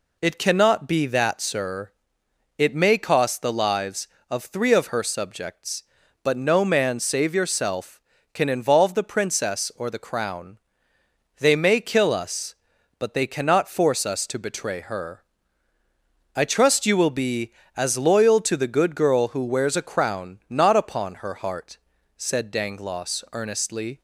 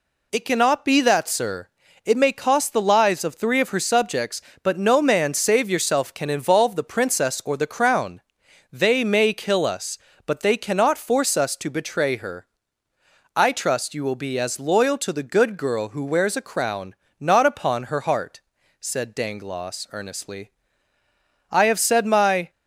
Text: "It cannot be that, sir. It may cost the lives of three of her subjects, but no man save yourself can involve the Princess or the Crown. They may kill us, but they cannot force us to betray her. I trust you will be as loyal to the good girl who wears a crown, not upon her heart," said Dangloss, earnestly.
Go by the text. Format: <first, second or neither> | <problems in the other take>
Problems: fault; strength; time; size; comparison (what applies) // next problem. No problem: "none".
first | goes on to say "I have said my"; noticeable; from 21.5 s on; 0.98 s long